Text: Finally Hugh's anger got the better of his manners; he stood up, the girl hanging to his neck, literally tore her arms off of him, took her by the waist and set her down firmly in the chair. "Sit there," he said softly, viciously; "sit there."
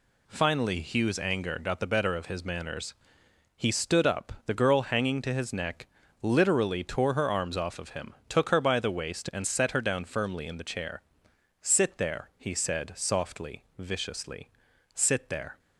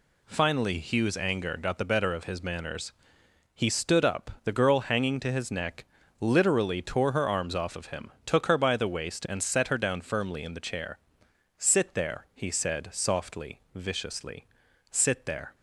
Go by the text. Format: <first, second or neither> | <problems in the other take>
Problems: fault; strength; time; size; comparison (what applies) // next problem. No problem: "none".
neither | none